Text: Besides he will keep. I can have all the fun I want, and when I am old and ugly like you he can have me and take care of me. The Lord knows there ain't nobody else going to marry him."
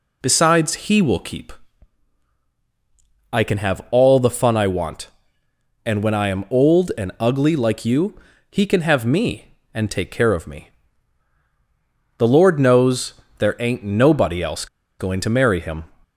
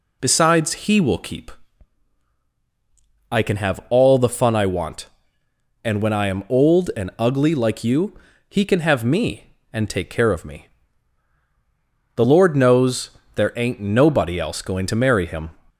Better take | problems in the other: second | pauses between "you" and "he"; slight; at 8.1 s; 0.36 s long; slight in the second // pauses between "knows" and "there"; slight; at 13.1 s; 0.24 s long; slight in the second // pauses between "else" and "going"; slight; at 14.6 s; 0.33 s long

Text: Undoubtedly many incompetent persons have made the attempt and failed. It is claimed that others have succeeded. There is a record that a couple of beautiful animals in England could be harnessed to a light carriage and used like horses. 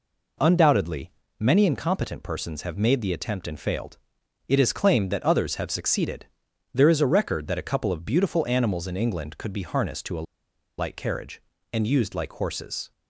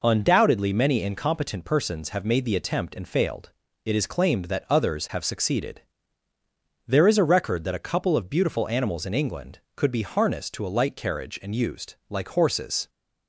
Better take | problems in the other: second | pauses between "Undoubtedly" and "many"; slight; at 1.1 s; 0.28 s long // pauses between "a" and "light"; noticeable; at 10.2 s; 0.53 s long

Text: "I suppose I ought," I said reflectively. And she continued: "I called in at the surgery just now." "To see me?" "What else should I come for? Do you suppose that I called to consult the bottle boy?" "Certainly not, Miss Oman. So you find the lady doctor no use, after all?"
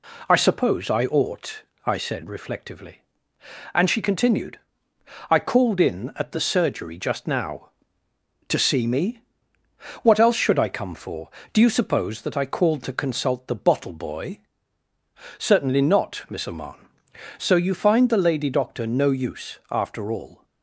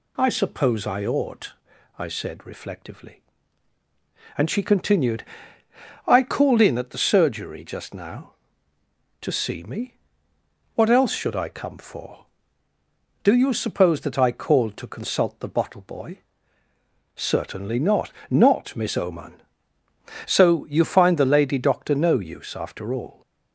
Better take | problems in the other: first | says "not" twice; at 18.2 s

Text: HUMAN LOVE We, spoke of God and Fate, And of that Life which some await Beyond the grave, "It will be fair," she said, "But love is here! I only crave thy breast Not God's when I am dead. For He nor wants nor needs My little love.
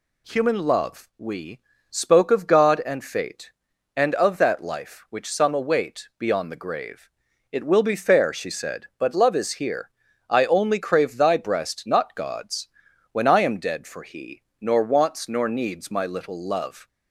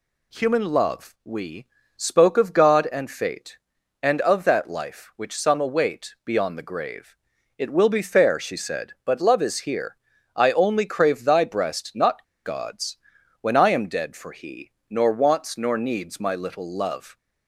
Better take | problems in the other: first | pauses between "Not" and "God's"; slight; at 12.2 s; 0.21 s long // pauses between "God's" and "when"; at 12.9 s; 0.42 s long; also in the first // pauses between "He" and "nor"; slight; at 14.7 s; 0.16 s long; slight in the first

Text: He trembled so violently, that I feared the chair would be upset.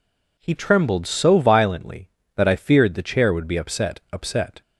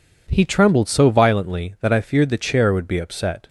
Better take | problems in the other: second | says "upset" twice; at 4.1 s

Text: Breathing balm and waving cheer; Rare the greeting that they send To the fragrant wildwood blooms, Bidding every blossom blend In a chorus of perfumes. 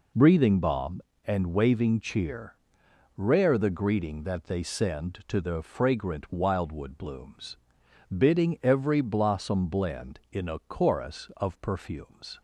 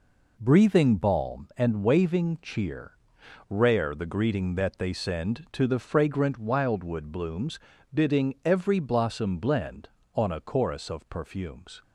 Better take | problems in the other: first | says "On" for "In"; at 10.1 s

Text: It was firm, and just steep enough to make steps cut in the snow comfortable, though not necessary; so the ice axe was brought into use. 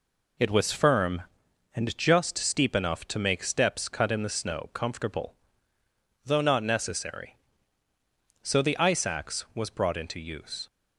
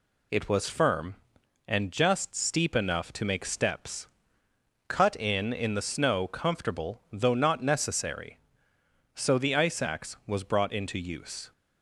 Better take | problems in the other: first | pauses between "steps" and "cut"; noticeable; at 4.0 s; 0.80 s long // says "in" twice; at 5.5 s

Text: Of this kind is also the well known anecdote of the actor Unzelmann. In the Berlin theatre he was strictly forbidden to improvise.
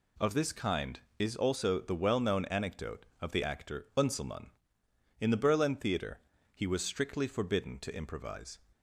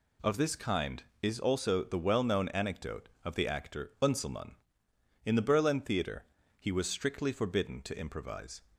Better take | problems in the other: neither | pauses between "theatre" and "he"; slight; the same in both

